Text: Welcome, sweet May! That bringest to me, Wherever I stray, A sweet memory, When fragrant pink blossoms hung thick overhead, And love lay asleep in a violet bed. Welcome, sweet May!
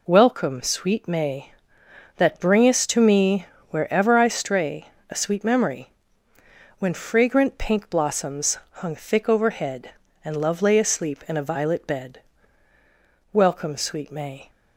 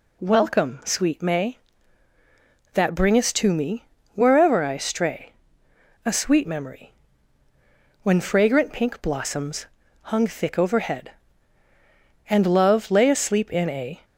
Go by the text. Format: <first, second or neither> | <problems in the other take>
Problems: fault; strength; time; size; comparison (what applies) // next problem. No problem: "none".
first | pauses between "blossoms" and "hung"; slight; at 9.6 s; 0.36 s long // stops before "violet bed Welcome sweet May"; at 14.0 s